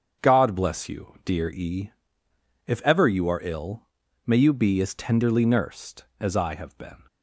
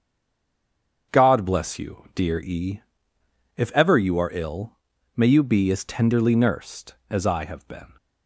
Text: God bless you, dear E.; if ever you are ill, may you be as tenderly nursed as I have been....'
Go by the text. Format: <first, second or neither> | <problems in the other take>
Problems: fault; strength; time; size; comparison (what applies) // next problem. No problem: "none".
first | stays silent before the first word; until 1.1 s; 1.1 s long // starts louder than the rest; strong; until 2.2 s; 7.5 dB; strong in the first